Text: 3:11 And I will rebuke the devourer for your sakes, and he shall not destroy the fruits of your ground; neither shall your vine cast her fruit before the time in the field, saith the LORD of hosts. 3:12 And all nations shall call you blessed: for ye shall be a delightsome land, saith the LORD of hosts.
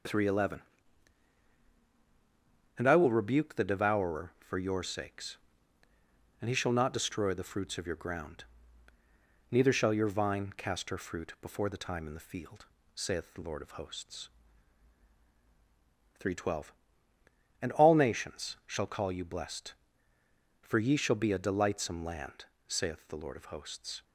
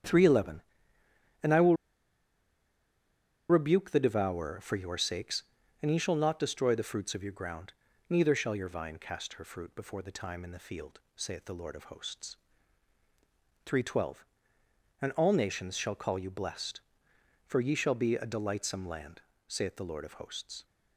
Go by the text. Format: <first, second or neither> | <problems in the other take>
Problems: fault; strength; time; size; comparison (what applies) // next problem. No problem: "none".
first | starts louder than the rest; strong; until 3.6 s; 9 dB; noticeable in the first // pauses between "will" and "rebuke"; strong; at 1.7 s; 1.7 s long